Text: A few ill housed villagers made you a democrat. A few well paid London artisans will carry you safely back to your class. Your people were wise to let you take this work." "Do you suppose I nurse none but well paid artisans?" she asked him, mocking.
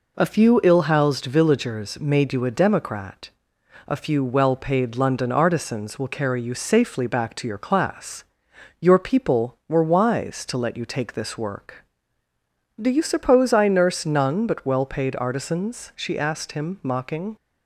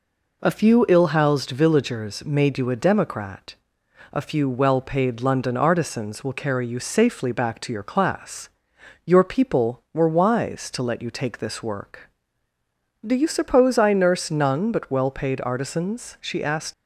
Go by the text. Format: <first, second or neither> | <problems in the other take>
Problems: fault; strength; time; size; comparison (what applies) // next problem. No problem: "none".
first | stops before "him mocking"; at 16.7 s